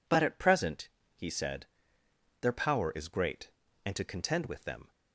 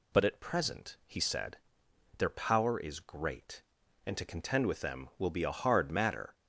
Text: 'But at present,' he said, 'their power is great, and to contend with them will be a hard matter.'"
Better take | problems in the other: second | stops before "will be a hard matter"; at 4.9 s

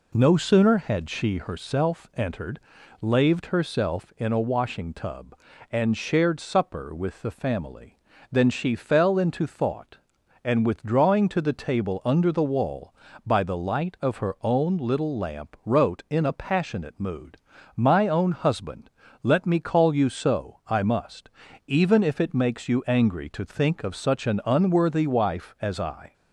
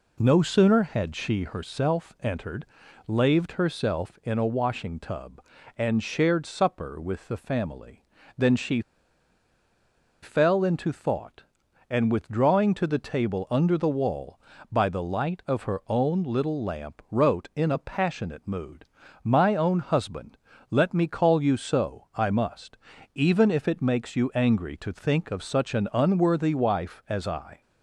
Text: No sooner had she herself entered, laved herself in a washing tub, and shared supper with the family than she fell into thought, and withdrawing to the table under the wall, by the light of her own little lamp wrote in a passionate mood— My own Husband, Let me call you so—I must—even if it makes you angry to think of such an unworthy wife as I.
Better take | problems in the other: first | pauses between "she" and "fell"; strong; at 8.8 s; 1.4 s long

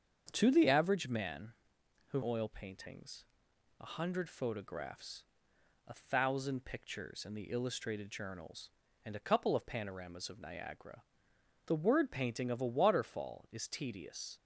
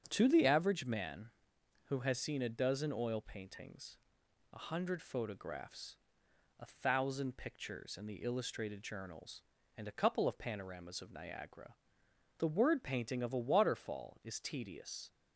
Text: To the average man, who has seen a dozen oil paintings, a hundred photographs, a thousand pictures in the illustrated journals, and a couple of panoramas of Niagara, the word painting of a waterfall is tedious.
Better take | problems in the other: second | starts louder than the rest; strong; until 1.3 s; 7 dB; strong in the second // skips "has seen a dozen"; at 2.2 s

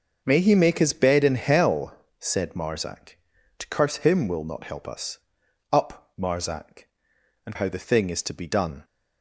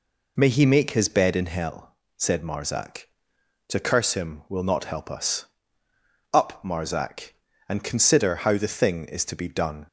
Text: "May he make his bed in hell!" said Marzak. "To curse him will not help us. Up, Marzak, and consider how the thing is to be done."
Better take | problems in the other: second | starts louder than the rest; until 1.2 s; 6.5 dB // skips "consider"; at 7.5 s

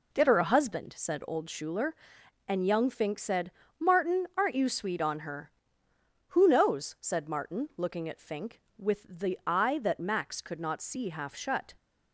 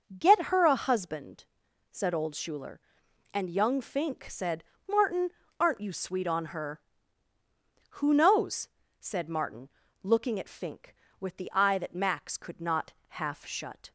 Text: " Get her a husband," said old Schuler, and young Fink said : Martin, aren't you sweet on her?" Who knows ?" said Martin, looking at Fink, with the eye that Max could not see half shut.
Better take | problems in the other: first | starts louder than the rest; until 1.0 s; 6 dB // skips "see"; at 13.0 s

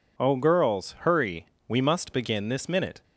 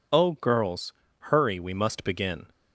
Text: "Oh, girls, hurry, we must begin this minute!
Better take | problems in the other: first | stops before "this minute"; at 2.4 s

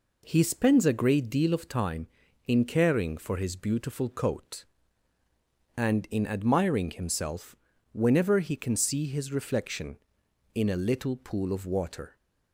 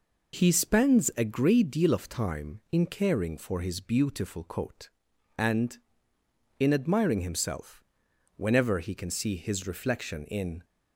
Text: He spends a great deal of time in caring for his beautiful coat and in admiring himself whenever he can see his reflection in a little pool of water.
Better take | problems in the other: first | pauses between "himself" and "whenever"; noticeable; at 7.8 s; 0.50 s long; slight in the first // stops before "a little pool of water"; at 10.6 s

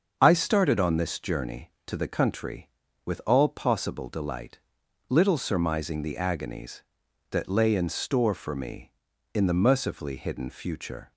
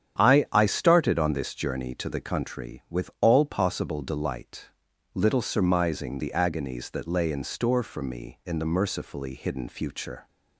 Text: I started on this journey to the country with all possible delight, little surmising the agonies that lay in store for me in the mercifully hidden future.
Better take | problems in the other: first | starts louder than the rest; strong; until 1.2 s; 9 dB; also in the first // says "I" twice; at 0.5 s

